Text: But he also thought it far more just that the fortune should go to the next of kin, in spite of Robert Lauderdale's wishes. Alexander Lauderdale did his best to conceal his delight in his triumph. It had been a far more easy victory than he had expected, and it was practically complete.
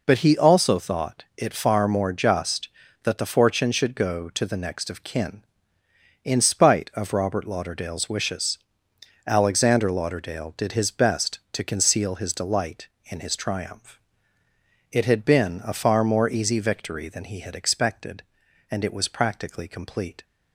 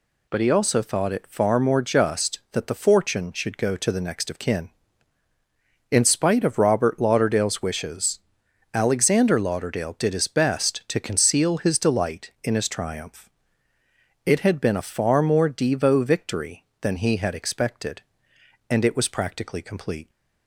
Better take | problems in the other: first | says "devo" for "easy"; at 15.4 s

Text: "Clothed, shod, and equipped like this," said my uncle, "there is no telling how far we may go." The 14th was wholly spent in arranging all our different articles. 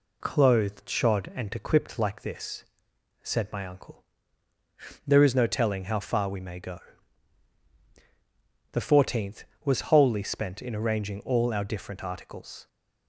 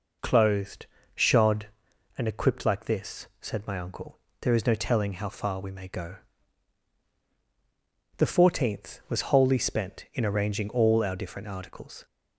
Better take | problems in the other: neither | none

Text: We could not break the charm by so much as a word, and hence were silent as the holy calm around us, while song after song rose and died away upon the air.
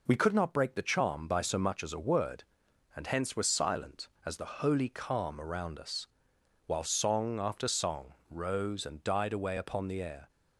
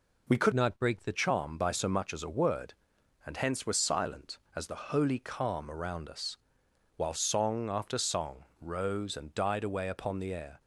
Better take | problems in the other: first | changes voice from "not" to "the"; from 0.5 to 1.1 s; 0.6 s long // pauses between "song" and "rose"; slight; at 8.4 s; 0.16 s long; slight in the first

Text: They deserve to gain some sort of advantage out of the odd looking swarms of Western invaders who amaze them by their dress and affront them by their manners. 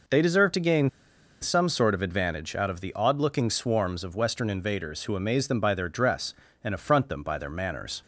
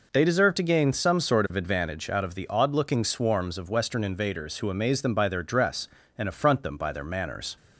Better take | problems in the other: second | pauses between "gain" and "some"; noticeable; at 0.8 s; 0.51 s long

